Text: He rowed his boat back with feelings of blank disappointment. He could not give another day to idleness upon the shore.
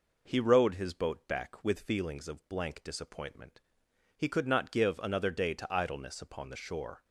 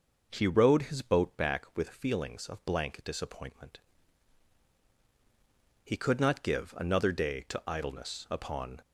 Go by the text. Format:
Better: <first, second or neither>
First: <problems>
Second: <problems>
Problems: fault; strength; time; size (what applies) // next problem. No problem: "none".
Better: first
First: none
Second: stops before "the shore"; at 8.8 s